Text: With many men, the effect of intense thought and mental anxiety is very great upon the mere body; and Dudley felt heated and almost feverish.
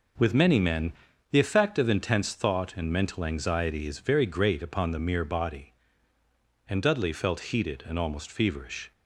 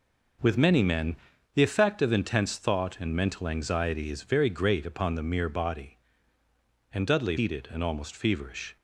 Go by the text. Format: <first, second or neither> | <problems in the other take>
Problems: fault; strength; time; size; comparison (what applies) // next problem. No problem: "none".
first | skips "felt"; at 7.3 s